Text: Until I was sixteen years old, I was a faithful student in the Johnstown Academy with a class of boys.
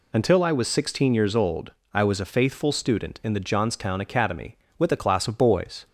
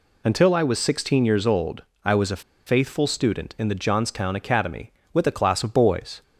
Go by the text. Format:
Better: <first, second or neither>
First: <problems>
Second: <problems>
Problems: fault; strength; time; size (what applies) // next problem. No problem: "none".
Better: first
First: none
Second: pauses between "a" and "faithful"; slight; at 2.4 s; 0.23 s long